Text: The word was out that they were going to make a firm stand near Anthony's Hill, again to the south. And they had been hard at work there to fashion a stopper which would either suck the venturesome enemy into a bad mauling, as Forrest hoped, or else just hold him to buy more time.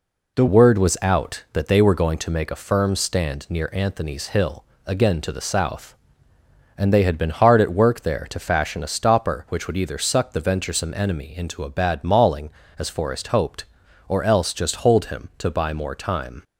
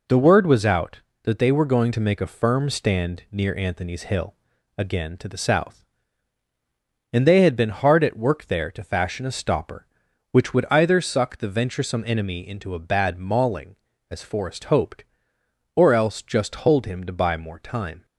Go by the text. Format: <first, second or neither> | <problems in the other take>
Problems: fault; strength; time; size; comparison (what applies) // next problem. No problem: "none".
second | changes voice at "word"; from 0.4 s on; 16.0 s long